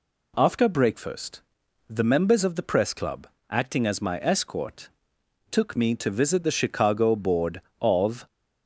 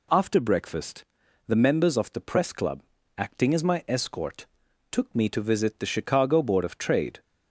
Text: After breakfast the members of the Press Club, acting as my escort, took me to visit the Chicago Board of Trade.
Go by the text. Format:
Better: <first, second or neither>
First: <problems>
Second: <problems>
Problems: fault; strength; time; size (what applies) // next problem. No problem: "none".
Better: second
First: pauses between "breakfast" and "the"; noticeable; at 1.4 s; 0.46 s long // stops before "Trade"; at 8.2 s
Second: pauses between "breakfast" and "the"; at 1.0 s; 0.44 s long